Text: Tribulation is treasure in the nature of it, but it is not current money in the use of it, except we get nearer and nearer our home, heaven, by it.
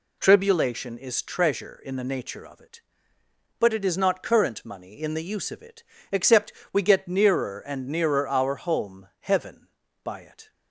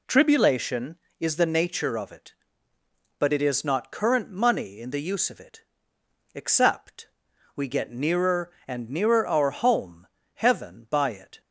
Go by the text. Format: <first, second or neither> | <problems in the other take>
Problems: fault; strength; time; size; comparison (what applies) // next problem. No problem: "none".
first | skips "treasure in"; at 1.3 s // pauses between "except" and "we"; noticeable; at 7.0 s; 0.48 s long; slight in the first